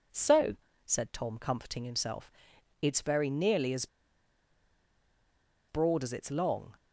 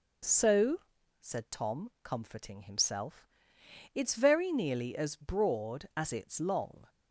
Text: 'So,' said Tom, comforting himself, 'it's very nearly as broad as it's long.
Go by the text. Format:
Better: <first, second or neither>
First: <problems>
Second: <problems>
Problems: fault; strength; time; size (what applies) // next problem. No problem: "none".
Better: second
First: pauses between "as" and "broad"; strong; at 3.8 s; 1.8 s long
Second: none